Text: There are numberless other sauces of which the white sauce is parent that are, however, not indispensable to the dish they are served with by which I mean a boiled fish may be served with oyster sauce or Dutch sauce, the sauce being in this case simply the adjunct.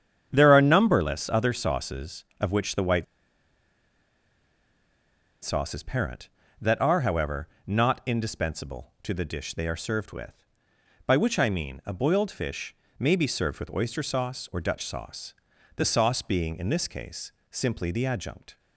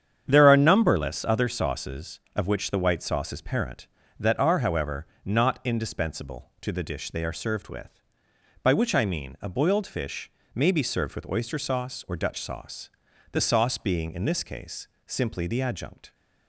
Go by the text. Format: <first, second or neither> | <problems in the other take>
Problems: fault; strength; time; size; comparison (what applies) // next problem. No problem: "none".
second | starts louder than the rest; strong; until 1.3 s; 8.5 dB; strong in the second // pauses between "white" and "sauce"; strong; at 3.0 s; 2.3 s long // pauses between "fish" and "may"; slight; at 12.7 s; 0.24 s long; slight in the second // pauses between "case" and "simply"; slight; at 17.3 s; 0.20 s long; slight in the second